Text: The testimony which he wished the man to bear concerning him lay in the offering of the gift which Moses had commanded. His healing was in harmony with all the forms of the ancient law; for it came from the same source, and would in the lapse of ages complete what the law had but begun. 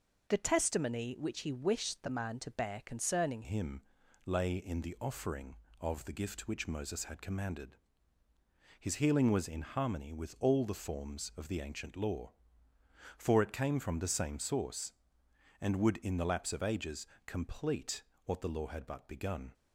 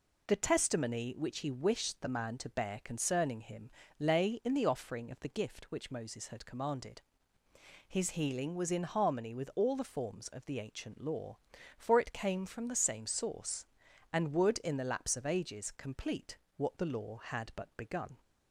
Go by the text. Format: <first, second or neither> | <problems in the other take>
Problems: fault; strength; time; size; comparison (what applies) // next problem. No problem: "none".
second | changes voice at "him"; from 3.4 s on; 16.1 s long // pauses between "him" and "lay"; at 3.8 s; 0.42 s long; slight in the second // pauses between "ages" and "complete"; slight; at 17.0 s; 0.20 s long // pauses between "complete" and "what"; slight; at 18.0 s; 0.22 s long; slight in the second